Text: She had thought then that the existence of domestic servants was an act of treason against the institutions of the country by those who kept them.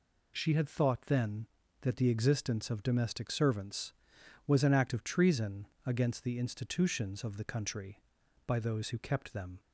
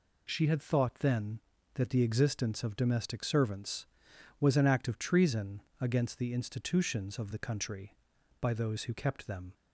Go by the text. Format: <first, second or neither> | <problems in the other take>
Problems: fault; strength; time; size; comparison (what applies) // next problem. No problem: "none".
neither | pauses between "treason" and "against"; slight; the same in both